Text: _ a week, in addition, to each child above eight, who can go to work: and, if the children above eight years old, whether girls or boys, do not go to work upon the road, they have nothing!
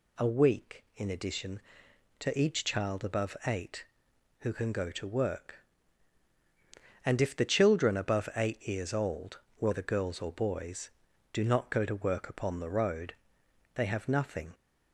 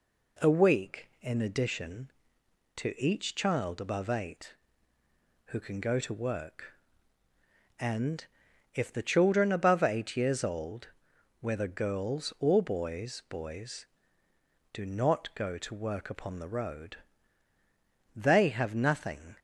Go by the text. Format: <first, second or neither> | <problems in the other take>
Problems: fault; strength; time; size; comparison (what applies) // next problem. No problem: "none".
first | says "boys" twice; at 13.2 s